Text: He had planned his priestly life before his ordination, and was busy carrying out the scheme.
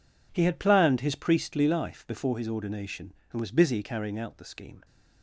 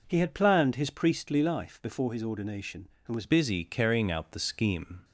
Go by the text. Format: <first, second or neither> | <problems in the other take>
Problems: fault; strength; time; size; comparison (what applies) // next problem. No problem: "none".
first | changes voice at "busy"; from 3.2 s on; 1.8 s long